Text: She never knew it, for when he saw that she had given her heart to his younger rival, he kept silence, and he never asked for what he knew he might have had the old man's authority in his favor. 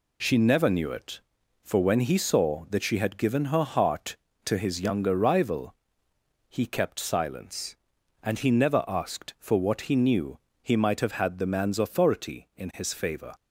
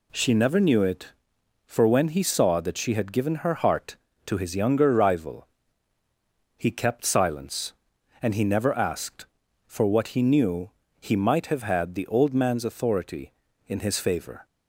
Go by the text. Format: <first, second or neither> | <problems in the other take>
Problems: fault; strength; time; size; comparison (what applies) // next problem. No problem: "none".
second | pauses between "knew" and "he"; slight; at 10.3 s; 0.24 s long; slight in the second // skips "old"; at 11.4 s